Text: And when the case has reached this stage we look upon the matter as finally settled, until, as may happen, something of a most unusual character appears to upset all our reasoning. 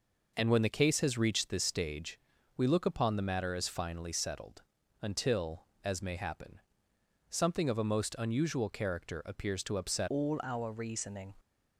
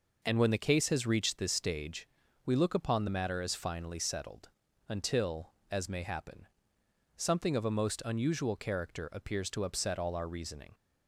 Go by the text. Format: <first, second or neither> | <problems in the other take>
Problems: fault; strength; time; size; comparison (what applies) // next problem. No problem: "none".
second | pauses between "stage" and "we"; at 2.1 s; 0.40 s long; also in the second // changes voice at "all"; from 10.0 s on; 1.3 s long